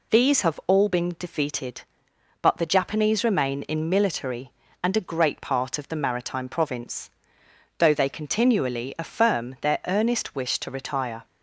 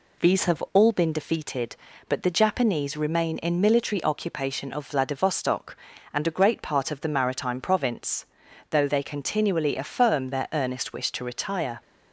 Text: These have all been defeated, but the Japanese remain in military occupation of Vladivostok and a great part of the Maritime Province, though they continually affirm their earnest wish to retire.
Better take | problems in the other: second | skips "occupation of Vladivostok"; at 4.6 s

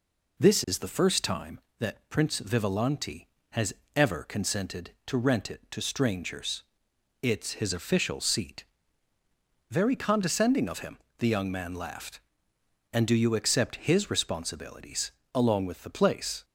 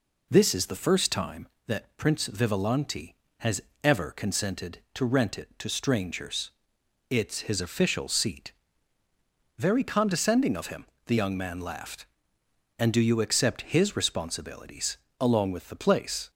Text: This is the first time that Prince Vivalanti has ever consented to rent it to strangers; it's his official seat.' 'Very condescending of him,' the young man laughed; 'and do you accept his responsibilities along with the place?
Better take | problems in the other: neither | pauses between "has" and "ever"; slight; the same in both // pauses between "responsibilities" and "along"; slight; the same in both

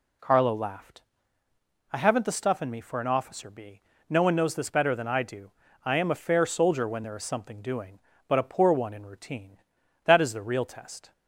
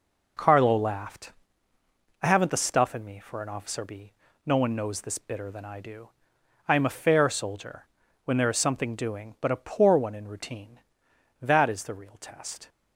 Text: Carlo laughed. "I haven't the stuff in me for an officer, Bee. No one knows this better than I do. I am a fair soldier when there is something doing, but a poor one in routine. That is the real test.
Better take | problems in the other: first | says "bitter" for "better"; at 5.1 s // pauses between "soldier" and "when"; at 7.8 s; 0.38 s long

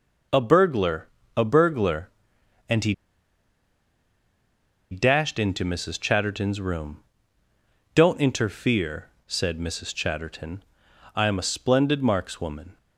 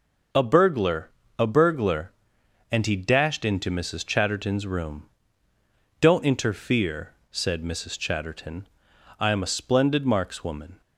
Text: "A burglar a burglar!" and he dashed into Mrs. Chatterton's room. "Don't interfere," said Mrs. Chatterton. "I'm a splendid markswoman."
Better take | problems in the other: second | pauses between "burglar" and "a"; slight; at 1.0 s; 0.26 s long; slight in the second // pauses between "he" and "dashed"; strong; at 2.9 s; 1.9 s long

